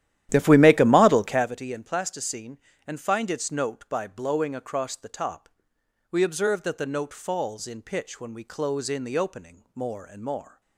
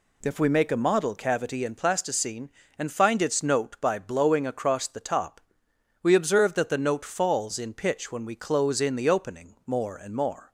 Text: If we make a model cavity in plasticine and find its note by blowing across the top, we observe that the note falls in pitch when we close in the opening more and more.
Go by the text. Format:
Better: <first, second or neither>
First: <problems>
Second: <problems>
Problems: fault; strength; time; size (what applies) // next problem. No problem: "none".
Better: second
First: starts louder than the rest; strong; until 1.6 s; 12 dB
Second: none